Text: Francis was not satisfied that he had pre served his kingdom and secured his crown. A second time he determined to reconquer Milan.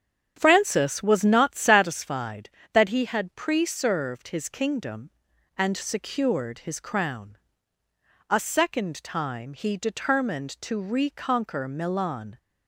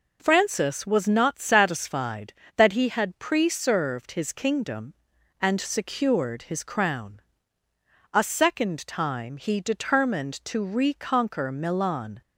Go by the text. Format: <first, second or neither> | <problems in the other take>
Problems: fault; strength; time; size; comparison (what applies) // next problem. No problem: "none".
second | starts louder than the rest; strong; until 1.9 s; 8 dB